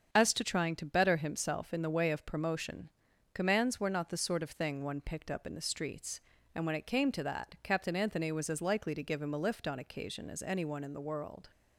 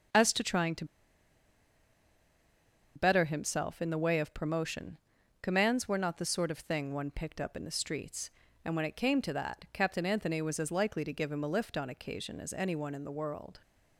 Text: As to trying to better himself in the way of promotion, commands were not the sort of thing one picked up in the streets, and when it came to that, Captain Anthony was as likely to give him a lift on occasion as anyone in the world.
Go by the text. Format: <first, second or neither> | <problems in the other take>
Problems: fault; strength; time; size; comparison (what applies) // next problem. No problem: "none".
first | starts louder than the rest; strong; until 3.2 s; 7.5 dB; strong in the first // pauses between "to" and "better"; strong; at 0.8 s; 2.1 s long